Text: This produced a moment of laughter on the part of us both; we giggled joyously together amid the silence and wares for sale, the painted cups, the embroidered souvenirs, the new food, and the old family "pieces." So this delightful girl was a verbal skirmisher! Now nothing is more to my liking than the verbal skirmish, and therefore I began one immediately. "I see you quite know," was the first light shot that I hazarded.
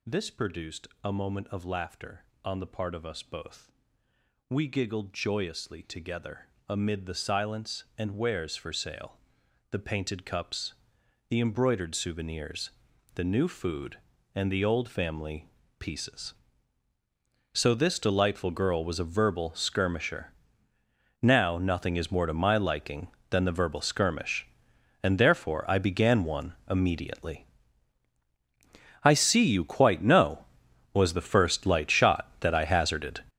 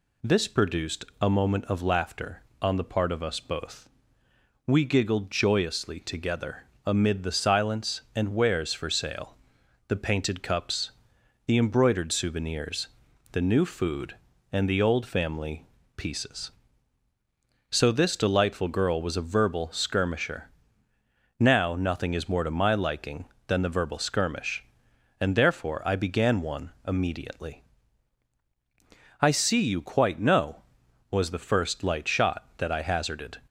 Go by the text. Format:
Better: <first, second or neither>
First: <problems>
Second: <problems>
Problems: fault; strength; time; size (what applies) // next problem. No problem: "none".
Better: second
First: gets louder; strong; throughout; 11.5 dB // pauses between "produced" and "a"; slight; at 0.8 s; 0.16 s long // pauses between "together" and "amid"; slight; at 6.4 s; 0.20 s long // pauses between "family" and "pieces"; slight; at 15.4 s; 0.28 s long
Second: pauses between "produced" and "a"; slight; at 1.0 s; 0.16 s long // pauses between "together" and "amid"; slight; at 6.6 s; 0.20 s long // pauses between "family" and "pieces"; slight; at 15.6 s; 0.28 s long